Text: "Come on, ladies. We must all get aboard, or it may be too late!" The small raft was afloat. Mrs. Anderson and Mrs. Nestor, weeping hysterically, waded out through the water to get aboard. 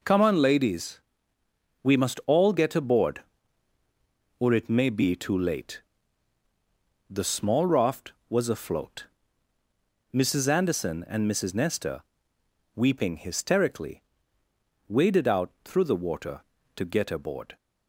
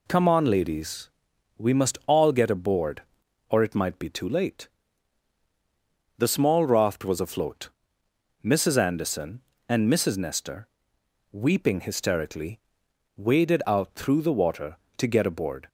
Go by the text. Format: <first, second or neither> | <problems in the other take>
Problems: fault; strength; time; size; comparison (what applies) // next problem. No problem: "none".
first | says "might" for "may"; at 3.7 s